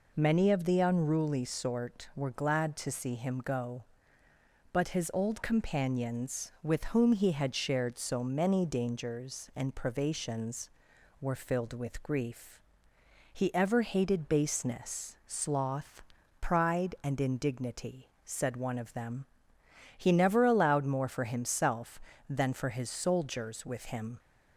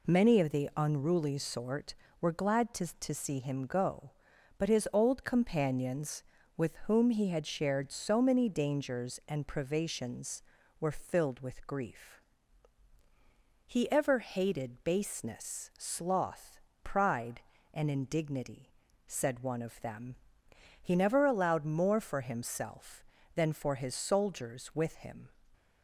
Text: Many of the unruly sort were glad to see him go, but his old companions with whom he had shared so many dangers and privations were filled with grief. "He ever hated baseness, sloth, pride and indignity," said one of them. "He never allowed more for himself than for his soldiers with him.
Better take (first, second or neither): first